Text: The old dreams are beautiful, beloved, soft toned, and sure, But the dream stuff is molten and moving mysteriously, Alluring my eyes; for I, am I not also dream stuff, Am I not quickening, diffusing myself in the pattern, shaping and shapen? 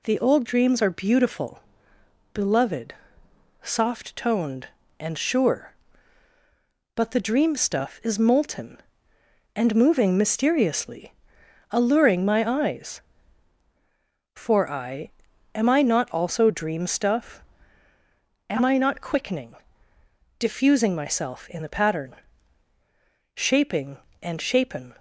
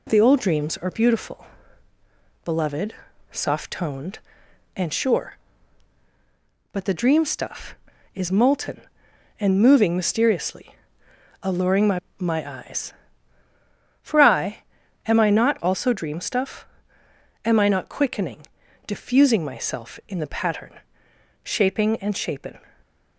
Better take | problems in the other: first | says "my" twice; at 12.1 s

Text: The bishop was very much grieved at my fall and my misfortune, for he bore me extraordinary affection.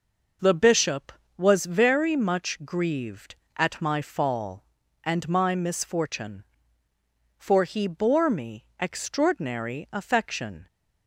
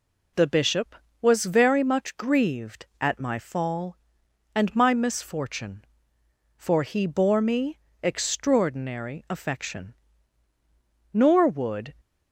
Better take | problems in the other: first | pauses between "me" and "extraordinary"; slight; at 7.7 s; 0.26 s long; slight in the first // goes on to say "Nor would"; noticeable; from 11.1 s on; 0.80 s long

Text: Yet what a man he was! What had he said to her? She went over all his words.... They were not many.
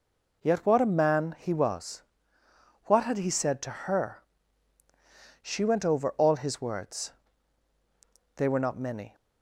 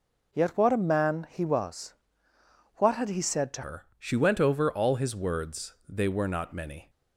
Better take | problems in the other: first | changes voice at "her"; from 3.6 s on; 3.2 s long

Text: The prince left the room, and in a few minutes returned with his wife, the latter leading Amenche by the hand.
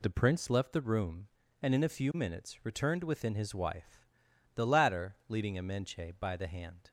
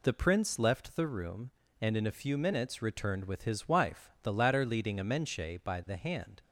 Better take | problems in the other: second | says "within" for "with"; at 3.0 s

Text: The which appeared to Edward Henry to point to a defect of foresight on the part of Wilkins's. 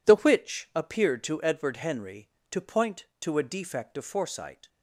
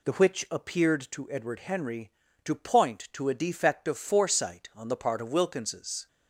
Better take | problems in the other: second | stops before "on the part of Wilkins's"; at 4.6 s

